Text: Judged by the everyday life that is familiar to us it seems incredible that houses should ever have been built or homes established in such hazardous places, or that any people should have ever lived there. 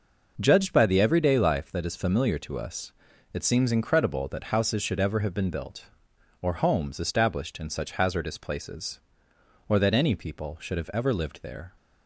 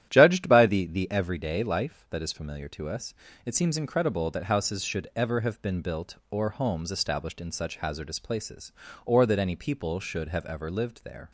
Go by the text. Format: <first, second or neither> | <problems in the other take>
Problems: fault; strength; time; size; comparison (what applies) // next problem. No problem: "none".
first | starts louder than the rest; strong; until 1.1 s; 11.5 dB // says "the" twice; at 0.8 s // pauses between "us" and "it"; slight; at 3.1 s; 0.32 s long; also in the first